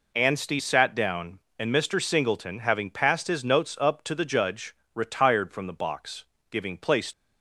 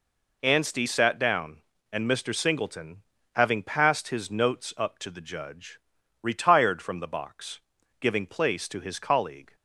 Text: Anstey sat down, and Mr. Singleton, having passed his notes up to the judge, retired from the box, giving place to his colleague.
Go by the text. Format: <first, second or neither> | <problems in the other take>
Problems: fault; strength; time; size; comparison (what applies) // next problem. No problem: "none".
second | stops before "to his colleague"; at 7.1 s